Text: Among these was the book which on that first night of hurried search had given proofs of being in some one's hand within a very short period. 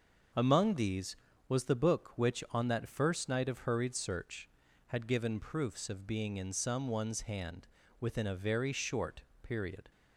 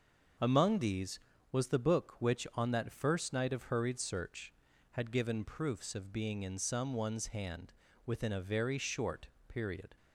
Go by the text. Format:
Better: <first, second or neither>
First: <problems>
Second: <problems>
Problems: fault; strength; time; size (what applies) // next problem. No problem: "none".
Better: neither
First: starts louder than the rest; until 1.6 s; 6 dB // pauses between "hand" and "within"; slight; at 7.6 s; 0.32 s long // pauses between "short" and "period"; slight; at 9.2 s; 0.20 s long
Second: starts louder than the rest; until 1.7 s; 6 dB // pauses between "hand" and "within"; slight; at 7.7 s; 0.32 s long // pauses between "short" and "period"; slight; at 9.2 s; 0.20 s long